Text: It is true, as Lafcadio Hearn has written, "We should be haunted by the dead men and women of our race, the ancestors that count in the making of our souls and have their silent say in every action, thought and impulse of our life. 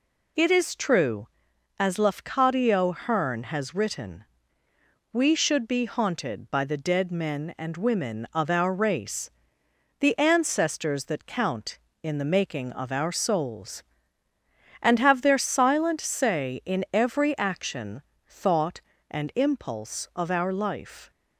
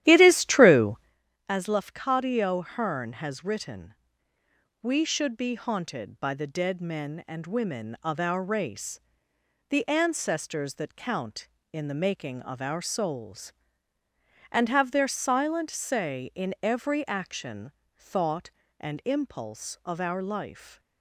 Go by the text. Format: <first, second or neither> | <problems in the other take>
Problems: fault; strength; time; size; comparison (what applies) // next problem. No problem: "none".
first | starts louder than the rest; strong; until 1.1 s; 12.5 dB